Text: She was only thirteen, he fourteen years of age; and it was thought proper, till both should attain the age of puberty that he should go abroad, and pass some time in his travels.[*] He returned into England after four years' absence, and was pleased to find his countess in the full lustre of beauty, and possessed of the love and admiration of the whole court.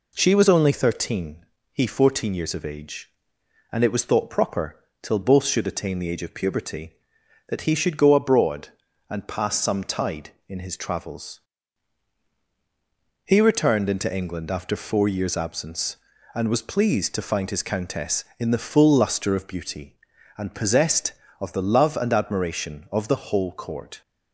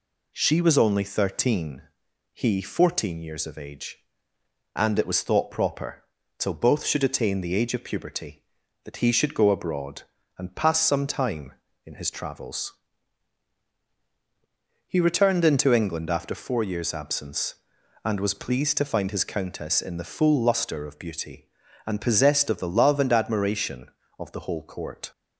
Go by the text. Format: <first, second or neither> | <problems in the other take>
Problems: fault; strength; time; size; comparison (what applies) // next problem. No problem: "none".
second | says "tide" for "time"; at 9.8 s